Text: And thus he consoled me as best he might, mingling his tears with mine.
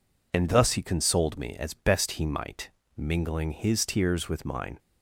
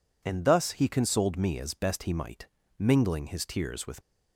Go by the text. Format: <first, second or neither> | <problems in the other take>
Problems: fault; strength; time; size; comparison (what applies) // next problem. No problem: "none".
first | stops before "mine"; at 4.0 s